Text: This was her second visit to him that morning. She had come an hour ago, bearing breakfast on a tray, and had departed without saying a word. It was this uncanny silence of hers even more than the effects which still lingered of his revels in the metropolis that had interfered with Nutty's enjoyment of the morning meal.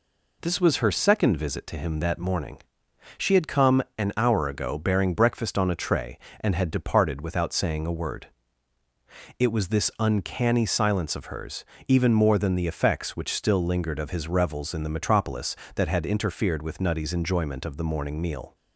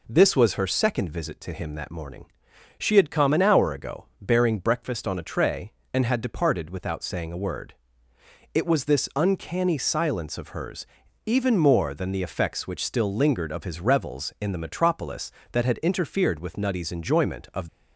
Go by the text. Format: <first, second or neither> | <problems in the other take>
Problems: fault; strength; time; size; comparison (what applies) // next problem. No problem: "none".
first | pauses between "hers" and "even"; at 10.8 s; 0.40 s long; slight in the first // stops before "the morning meal"; at 17.6 s